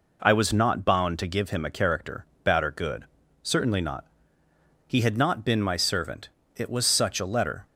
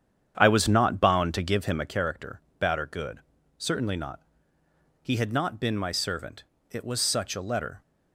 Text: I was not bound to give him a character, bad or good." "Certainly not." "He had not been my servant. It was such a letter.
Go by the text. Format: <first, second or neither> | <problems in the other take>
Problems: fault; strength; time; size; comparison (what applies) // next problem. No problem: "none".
first | starts louder than the rest; strong; until 2.0 s; 8.5 dB